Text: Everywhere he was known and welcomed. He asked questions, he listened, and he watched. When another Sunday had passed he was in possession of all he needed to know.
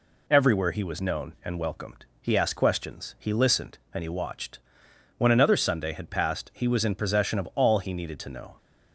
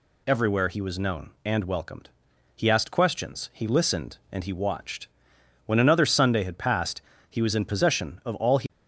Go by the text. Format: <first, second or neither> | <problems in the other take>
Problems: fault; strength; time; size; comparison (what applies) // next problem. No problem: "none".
first | pauses between "passed" and "he"; slight; at 7.0 s; 0.28 s long // stops before "needed to know"; at 8.6 s